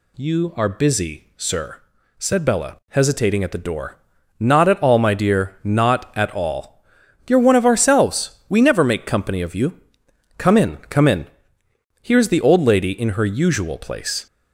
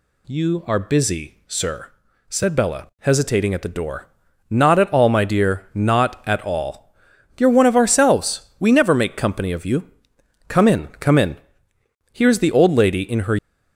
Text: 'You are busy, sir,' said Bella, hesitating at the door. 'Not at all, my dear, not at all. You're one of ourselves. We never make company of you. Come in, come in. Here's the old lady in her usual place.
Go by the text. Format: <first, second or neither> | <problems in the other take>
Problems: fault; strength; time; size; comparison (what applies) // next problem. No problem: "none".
first | stops before "usual place"; at 13.3 s